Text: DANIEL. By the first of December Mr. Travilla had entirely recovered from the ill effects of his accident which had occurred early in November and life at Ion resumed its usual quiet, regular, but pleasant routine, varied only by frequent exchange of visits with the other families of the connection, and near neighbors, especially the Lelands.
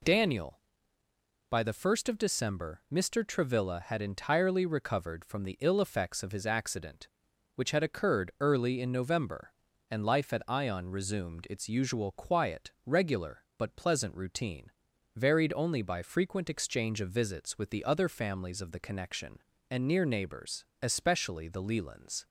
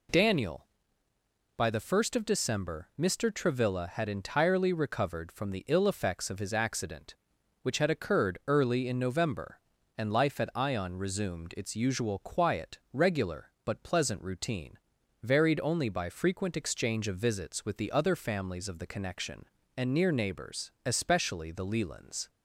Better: neither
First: none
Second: none

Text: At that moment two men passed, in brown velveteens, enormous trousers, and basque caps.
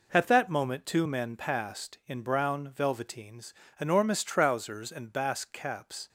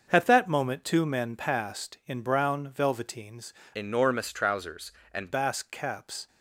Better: first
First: none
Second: starts louder than the rest; until 1.1 s; 6.5 dB // changes voice from "enormous" to "and"; from 3.7 to 5.3 s; 1.6 s long

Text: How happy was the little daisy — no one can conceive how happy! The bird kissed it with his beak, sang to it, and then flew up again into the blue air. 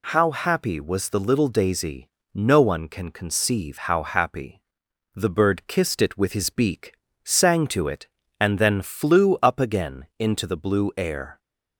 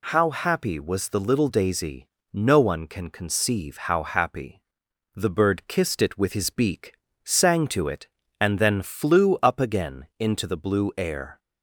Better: neither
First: none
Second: none

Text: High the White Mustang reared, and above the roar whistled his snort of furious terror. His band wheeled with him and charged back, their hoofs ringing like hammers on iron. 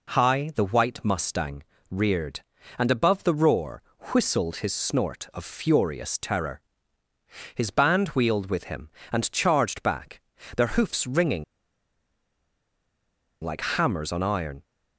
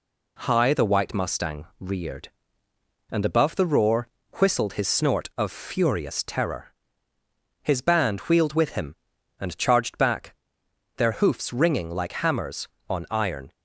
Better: second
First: pauses between "Mustang" and "reared"; slight; at 1.6 s; 0.28 s long // pauses between "roar" and "whistled"; slight; at 3.8 s; 0.28 s long // pauses between "ringing" and "like"; strong; at 11.4 s; 1.9 s long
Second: pauses between "roar" and "whistled"; slight; at 4.0 s; 0.32 s long

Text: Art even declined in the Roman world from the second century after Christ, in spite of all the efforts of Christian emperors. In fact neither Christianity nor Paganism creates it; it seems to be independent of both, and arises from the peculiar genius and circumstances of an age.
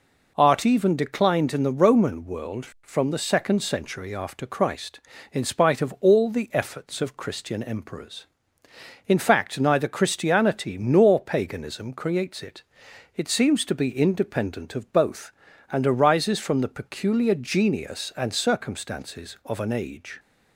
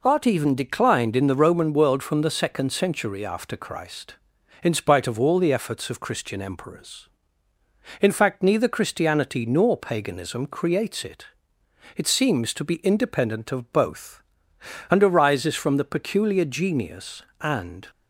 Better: first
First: none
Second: stops before "circumstances of an age"; at 17.8 s

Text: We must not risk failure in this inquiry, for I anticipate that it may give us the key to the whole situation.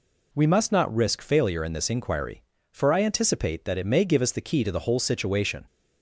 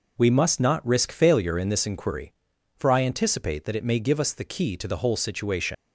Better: first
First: none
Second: leaves "situation" unfinished; at 5.7 s; 145 ms

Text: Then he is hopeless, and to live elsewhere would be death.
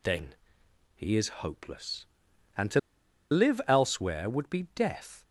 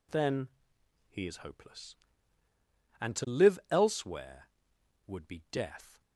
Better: second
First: pauses between "Then" and "he"; noticeable; at 0.3 s; 0.62 s long // pauses between "to" and "live"; noticeable; at 2.7 s; 0.51 s long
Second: pauses between "Then" and "he"; noticeable; at 0.4 s; 0.60 s long

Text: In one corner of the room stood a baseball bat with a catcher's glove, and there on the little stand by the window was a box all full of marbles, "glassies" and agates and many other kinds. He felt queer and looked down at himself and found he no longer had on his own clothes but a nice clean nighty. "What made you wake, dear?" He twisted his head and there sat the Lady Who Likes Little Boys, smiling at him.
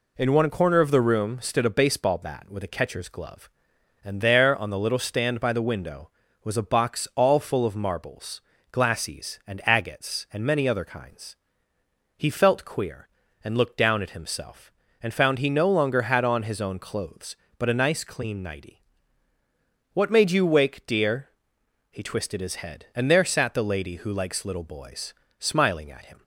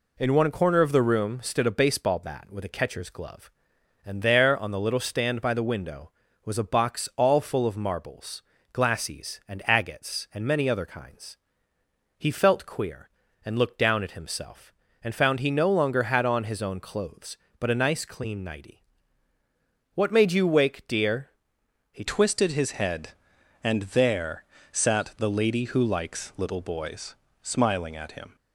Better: first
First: none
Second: changes voice at "twisted"; from 22.0 s on; 6.3 s long // pauses between "there" and "sat"; slight; at 24.4 s; 0.30 s long

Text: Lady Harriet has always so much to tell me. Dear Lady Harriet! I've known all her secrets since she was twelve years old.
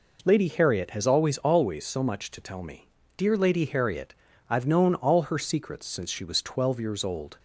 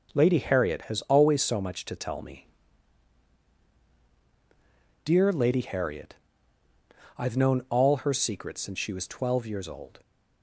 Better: second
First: says "always" twice; at 1.3 s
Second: none

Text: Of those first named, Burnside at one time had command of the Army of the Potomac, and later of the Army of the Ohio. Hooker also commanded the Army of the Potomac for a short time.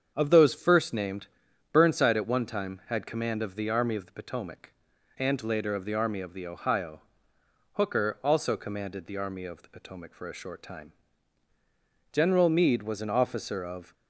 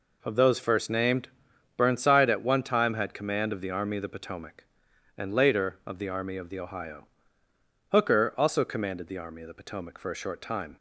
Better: second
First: starts louder than the rest; strong; until 1.1 s; 7.5 dB // goes on to say "General Meade was an officer of"; strong; from 12.1 s on; 1.8 s long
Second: none

